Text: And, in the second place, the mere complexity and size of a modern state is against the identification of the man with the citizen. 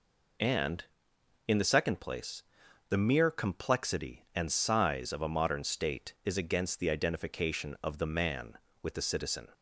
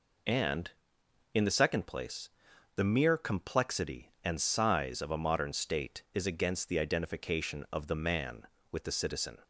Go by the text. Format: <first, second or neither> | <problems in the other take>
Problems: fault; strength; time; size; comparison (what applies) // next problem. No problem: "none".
neither | none